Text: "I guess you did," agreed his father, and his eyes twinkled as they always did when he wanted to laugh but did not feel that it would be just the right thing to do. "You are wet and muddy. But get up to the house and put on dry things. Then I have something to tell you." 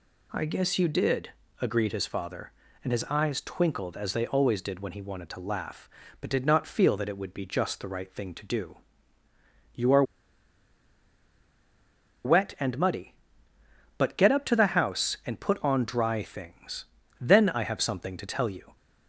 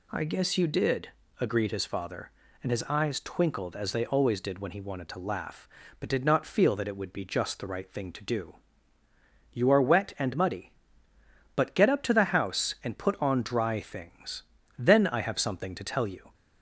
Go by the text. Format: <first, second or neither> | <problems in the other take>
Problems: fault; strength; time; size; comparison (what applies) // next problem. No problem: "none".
second | pauses between "are" and "wet"; strong; at 10.0 s; 2.2 s long